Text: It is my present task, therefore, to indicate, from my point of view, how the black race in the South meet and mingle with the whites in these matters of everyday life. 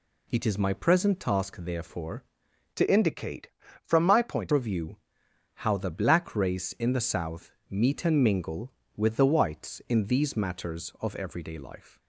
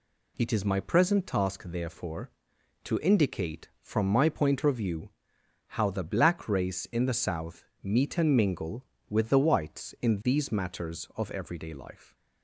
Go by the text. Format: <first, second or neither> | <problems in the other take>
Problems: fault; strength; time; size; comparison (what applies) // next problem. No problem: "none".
second | changes voice from "to" to "point"; from 2.7 to 4.5 s; 1.8 s long // pauses between "South" and "meet"; slight; at 7.5 s; 0.18 s long; slight in the second